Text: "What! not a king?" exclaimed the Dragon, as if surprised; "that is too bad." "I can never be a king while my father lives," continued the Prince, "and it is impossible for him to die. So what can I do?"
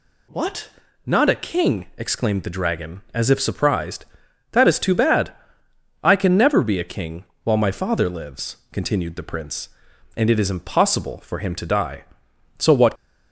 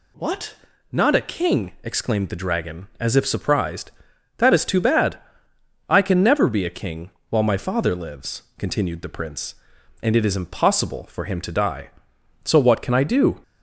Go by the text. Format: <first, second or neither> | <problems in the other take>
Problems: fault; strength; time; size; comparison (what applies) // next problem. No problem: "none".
second | pauses between "king" and "while"; slight; at 7.2 s; 0.22 s long; slight in the second // stops before "can I do"; at 12.9 s